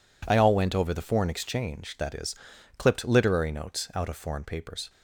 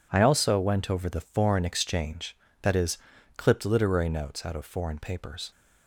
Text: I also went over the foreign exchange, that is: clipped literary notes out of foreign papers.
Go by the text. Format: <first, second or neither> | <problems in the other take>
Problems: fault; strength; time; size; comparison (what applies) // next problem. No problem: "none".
second | says "all" for "also"; at 0.3 s